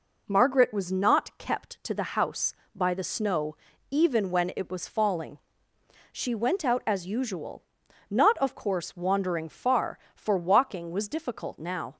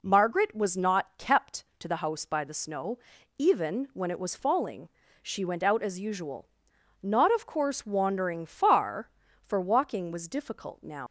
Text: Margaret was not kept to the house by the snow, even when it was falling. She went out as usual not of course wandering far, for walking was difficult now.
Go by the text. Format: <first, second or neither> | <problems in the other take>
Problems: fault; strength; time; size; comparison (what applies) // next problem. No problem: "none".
first | pauses between "usual" and "not"; noticeable; at 6.4 s; 0.56 s long; noticeable in the first // leaves "now" unfinished; at 11.0 s; 100 ms